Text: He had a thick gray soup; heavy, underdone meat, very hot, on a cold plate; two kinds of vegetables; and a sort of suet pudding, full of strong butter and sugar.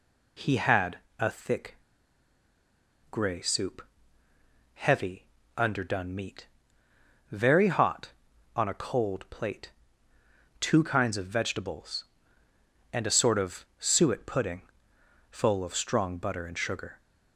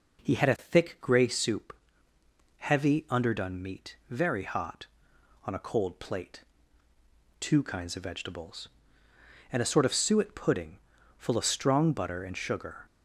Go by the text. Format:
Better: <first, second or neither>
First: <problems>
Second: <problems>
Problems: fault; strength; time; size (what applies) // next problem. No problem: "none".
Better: second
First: pauses between "had" and "a"; slight; at 0.9 s; 0.20 s long // pauses between "thick" and "gray"; strong; at 1.7 s; 1.3 s long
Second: none